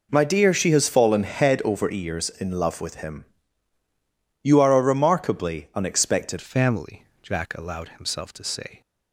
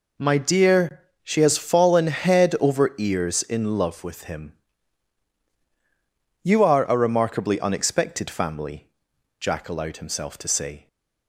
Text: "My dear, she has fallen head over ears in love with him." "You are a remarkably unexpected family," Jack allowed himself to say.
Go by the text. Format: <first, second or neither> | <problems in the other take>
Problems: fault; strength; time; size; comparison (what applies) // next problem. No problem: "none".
second | changes voice at "family"; from 6.4 s on; 2.4 s long